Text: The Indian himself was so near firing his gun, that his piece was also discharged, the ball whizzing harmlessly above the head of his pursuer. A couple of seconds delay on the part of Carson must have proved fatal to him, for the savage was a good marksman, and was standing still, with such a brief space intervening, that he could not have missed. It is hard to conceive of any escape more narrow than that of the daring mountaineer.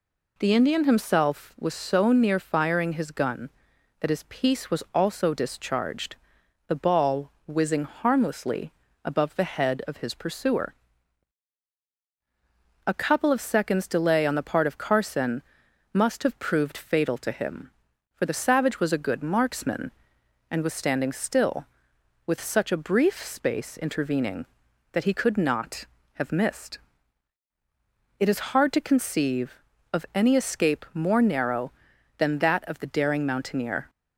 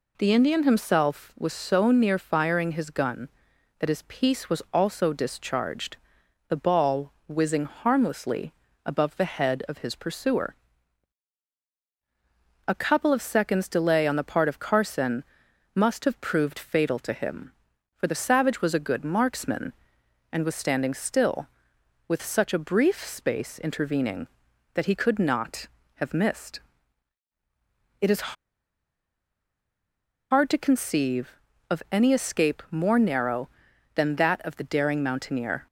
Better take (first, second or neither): first